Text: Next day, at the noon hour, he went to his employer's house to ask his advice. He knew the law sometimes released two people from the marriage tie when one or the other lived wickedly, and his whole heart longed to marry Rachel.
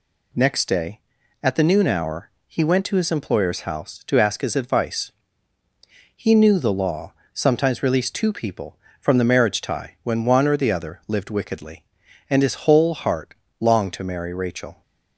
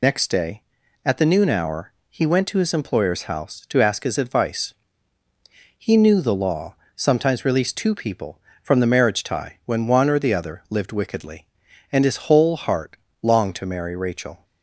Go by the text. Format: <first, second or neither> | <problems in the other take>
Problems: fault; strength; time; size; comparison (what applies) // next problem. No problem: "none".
first | loses the start of "Next"; at 0.0 s; 70 ms // pauses between "law" and "sometimes"; slight; at 6.7 s; 0.22 s long; slight in the first // pauses between "heart" and "longed"; slight; at 12.9 s; 0.26 s long; slight in the first